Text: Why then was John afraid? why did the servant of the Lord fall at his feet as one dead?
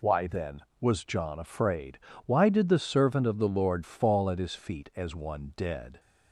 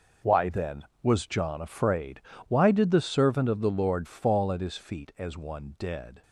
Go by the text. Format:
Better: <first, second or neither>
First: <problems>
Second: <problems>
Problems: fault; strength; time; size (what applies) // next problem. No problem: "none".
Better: first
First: none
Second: gets quieter; strong; throughout; 11 dB